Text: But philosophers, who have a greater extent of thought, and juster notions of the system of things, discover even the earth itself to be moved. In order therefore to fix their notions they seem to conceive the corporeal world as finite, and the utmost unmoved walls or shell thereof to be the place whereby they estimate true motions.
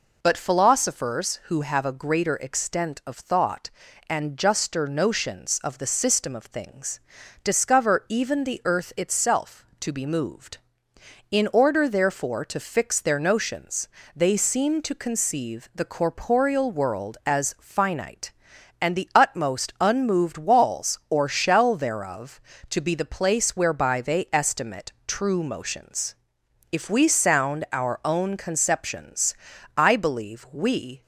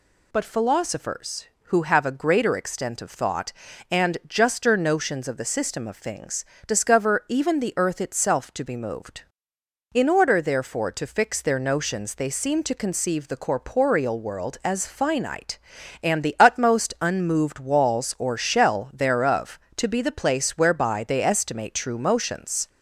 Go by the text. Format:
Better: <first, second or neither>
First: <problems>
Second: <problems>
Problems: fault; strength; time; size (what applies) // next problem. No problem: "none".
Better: second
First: pauses between "notions" and "they"; slight; at 13.8 s; 0.30 s long // pauses between "estimate" and "true"; slight; at 24.9 s; 0.16 s long // goes on to say "If we sound our own conceptions I believe we"; strong; from 26.7 s on; 4.3 s long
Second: none